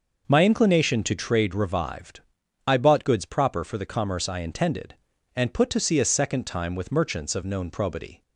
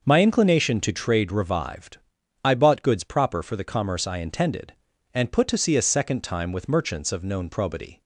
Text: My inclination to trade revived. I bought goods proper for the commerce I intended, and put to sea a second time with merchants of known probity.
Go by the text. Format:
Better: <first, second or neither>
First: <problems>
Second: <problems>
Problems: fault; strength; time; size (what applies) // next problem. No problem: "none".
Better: neither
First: none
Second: none